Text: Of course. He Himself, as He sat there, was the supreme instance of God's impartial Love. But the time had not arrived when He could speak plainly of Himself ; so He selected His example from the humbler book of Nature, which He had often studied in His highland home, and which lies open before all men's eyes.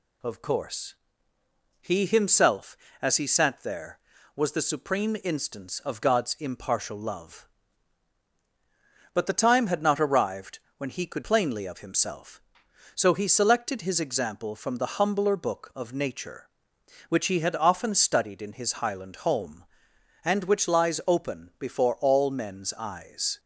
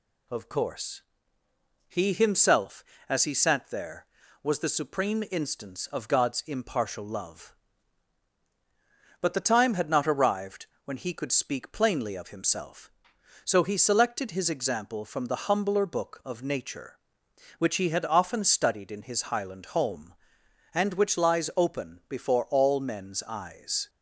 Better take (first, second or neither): second